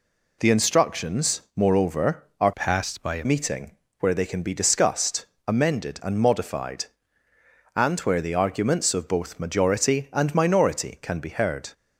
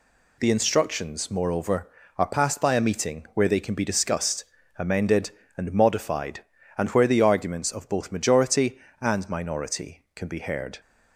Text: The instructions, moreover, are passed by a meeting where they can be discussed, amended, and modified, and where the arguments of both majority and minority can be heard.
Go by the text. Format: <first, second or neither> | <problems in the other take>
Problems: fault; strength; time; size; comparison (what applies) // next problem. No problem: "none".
second | changes voice from "passed" to "a"; from 2.5 to 3.2 s; 0.7 s long // pauses between "meeting" and "where"; slight; at 3.7 s; 0.30 s long